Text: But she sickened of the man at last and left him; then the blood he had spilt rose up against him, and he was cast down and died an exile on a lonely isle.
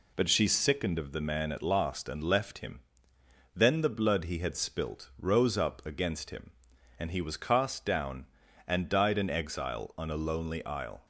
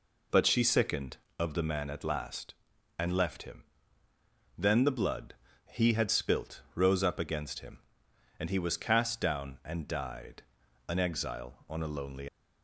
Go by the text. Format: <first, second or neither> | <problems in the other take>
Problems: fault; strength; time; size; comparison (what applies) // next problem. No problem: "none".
first | pauses between "blood" and "he"; slight; at 5.3 s; 0.36 s long // pauses between "died" and "an"; at 10.4 s; 0.44 s long // stops before "isle"; at 12.2 s